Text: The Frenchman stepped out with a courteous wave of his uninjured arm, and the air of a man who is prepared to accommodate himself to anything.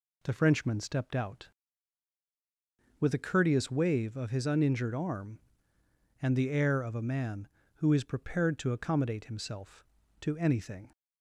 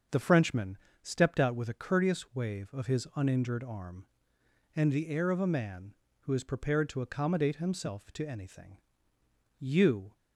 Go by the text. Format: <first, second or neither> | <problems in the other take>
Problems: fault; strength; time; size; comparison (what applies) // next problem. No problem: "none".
first | starts louder than the rest; until 1.3 s; 6.5 dB // pauses between "Frenchman" and "stepped"; slight; at 0.7 s; 0.26 s long // goes on to say "You"; from 9.5 s on; 0.54 s long